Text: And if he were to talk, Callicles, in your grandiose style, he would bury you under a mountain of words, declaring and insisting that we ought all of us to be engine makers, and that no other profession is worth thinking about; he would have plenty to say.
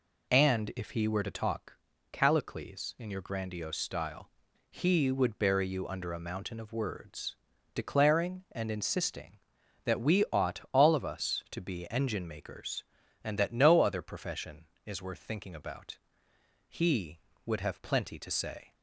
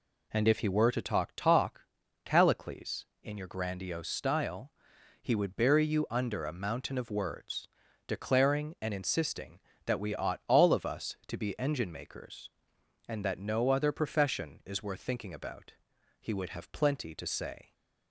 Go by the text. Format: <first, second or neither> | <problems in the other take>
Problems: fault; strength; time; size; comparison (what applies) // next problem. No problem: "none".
first | says "talk" twice; at 1.3 s